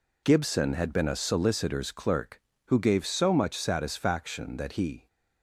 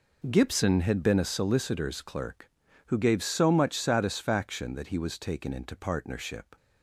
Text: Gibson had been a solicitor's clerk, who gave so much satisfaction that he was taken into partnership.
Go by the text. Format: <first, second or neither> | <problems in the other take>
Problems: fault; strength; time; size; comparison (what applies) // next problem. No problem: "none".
second | stops before "was taken into partnership"; at 5.0 s